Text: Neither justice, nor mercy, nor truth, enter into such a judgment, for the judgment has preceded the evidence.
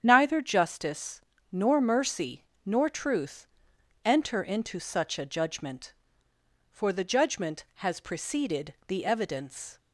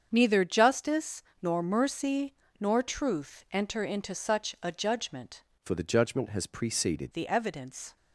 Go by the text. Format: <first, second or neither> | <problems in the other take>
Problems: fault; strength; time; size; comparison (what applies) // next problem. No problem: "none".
first | starts louder than the rest; strong; until 1.1 s; 7.5 dB; strong in the first // changes voice from "for" to "preceded"; from 5.6 to 7.1 s; 1.5 s long